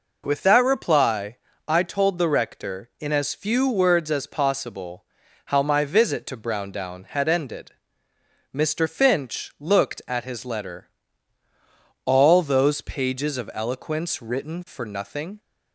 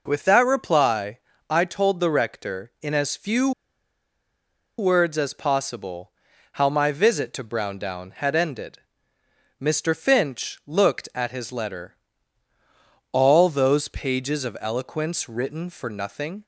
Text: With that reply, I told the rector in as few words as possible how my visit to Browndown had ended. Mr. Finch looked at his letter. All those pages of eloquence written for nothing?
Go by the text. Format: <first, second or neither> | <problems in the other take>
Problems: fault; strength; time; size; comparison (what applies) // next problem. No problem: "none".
first | pauses between "few" and "words"; strong; at 3.5 s; 1.2 s long // pauses between "possible" and "how"; at 6.1 s; 0.42 s long; also in the first